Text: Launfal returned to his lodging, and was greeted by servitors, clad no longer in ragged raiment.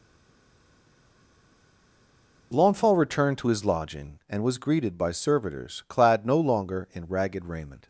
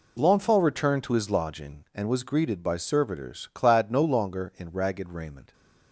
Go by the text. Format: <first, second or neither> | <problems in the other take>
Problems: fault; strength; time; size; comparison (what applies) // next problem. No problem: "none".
second | stays silent before the first word; until 2.5 s; 2.5 s long